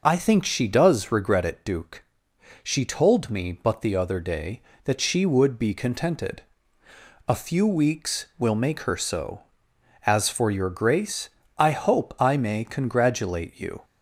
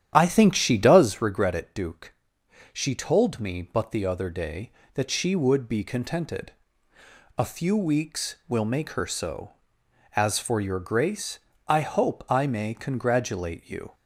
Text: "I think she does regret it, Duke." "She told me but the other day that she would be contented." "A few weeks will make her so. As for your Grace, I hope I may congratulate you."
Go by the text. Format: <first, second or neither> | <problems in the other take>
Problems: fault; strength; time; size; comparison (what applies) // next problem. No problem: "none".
first | starts louder than the rest; strong; until 1.2 s; 10.5 dB